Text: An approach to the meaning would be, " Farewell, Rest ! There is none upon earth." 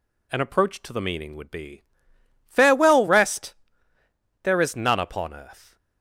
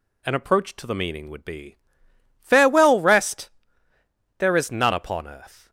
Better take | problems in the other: neither | none

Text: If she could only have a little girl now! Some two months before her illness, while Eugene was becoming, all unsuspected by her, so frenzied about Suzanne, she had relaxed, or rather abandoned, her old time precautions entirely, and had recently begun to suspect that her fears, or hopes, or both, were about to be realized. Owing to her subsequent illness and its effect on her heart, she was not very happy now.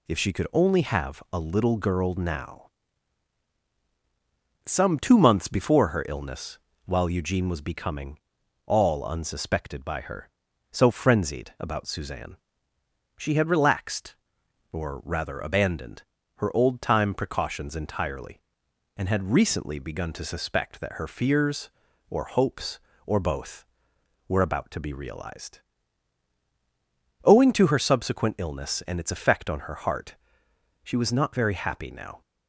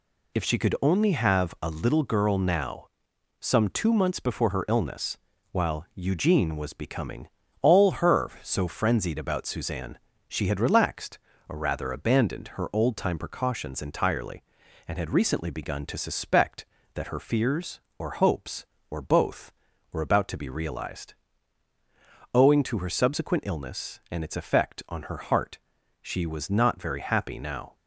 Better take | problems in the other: first | skips "unsuspected by"; at 7.9 s

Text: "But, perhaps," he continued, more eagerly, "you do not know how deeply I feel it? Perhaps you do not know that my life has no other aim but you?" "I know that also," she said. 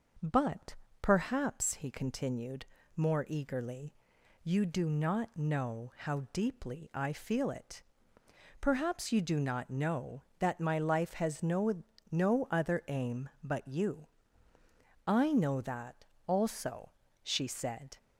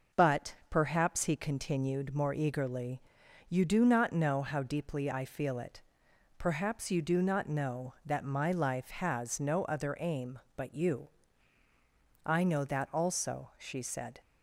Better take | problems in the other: second | says "no" twice; at 12.0 s // pauses between "that" and "also"; slight; at 16.0 s; 0.22 s long

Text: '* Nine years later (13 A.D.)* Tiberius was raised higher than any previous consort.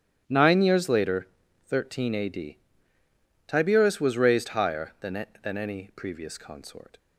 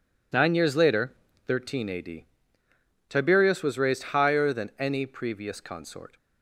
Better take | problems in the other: second | starts louder than the rest; strong; until 1.2 s; 10 dB // says "than" twice; at 5.4 s

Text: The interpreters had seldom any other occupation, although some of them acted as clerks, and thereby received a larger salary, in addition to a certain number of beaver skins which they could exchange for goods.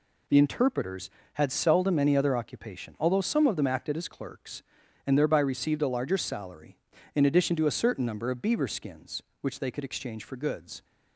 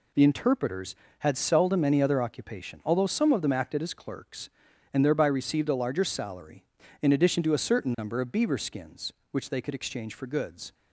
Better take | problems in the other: neither | none

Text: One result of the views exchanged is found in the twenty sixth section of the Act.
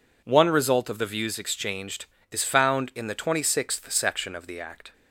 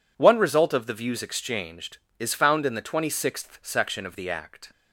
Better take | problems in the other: neither | none

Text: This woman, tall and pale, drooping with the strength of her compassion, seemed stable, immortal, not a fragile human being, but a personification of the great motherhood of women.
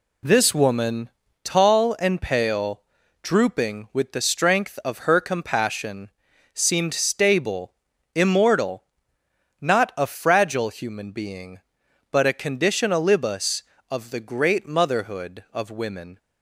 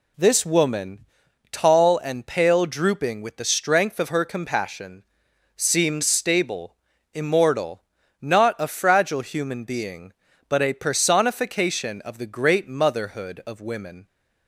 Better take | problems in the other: second | says "conditionalibus" for "personification"; at 12.3 s

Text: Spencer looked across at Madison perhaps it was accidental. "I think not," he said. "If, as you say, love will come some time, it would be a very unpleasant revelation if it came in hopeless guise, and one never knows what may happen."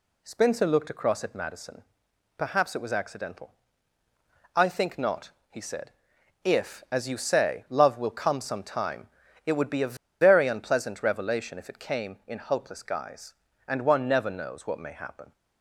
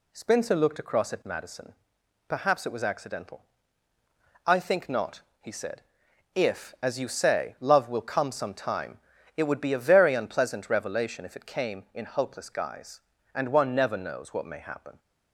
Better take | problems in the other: second | pauses between "Madison" and "perhaps"; noticeable; at 1.8 s; 0.56 s long; noticeable in the second // pauses between "a" and "very"; slight; at 9.9 s; 0.27 s long

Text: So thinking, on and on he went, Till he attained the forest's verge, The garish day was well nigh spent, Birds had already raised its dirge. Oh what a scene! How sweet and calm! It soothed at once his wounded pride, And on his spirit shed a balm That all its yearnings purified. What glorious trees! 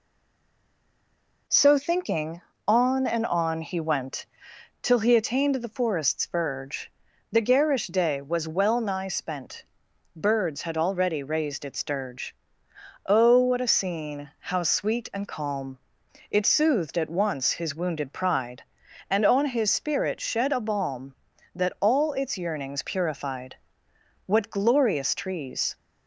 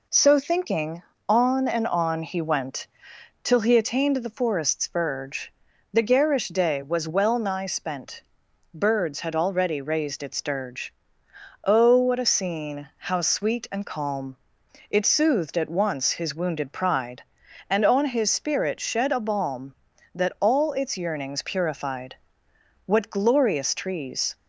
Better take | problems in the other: second | stays silent before the first word; noticeable; until 1.4 s; 1.4 s long

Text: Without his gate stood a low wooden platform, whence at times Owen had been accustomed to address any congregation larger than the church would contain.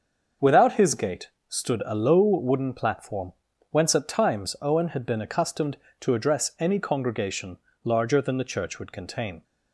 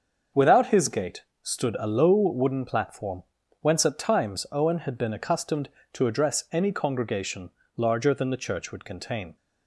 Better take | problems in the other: neither | starts louder than the rest; the same in both // pauses between "gate" and "stood"; slight; the same in both // pauses between "congregation" and "larger"; slight; the same in both

